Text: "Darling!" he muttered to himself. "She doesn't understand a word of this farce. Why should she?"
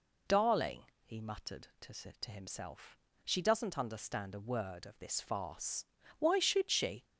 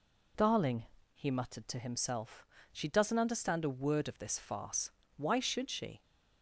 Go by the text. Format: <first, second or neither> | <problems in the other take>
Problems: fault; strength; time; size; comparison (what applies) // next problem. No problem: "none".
second | says "to" twice; at 1.9 s